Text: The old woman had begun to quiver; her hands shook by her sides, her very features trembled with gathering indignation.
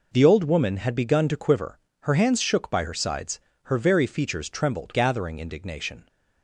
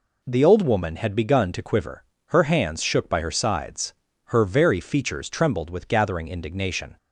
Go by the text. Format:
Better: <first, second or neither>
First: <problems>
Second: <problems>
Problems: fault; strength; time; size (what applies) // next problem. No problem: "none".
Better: second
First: skips "with"; at 4.9 s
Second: none